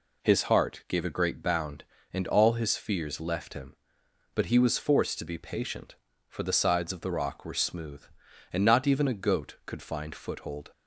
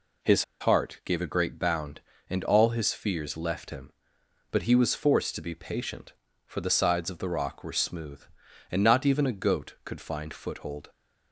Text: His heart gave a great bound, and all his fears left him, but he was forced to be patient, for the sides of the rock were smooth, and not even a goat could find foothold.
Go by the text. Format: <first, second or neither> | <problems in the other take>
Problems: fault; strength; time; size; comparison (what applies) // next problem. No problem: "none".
first | pauses between "His" and "heart"; slight; at 0.4 s; 0.16 s long